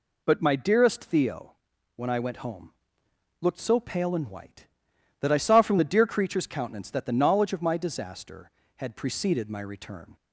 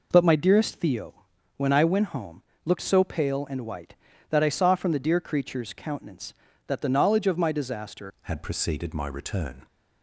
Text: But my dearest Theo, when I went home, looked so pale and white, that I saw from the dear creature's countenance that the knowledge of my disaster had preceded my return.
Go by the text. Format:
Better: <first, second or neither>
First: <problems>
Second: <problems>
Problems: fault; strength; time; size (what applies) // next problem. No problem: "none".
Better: first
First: none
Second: changes voice at "had"; from 8.2 s on; 1.4 s long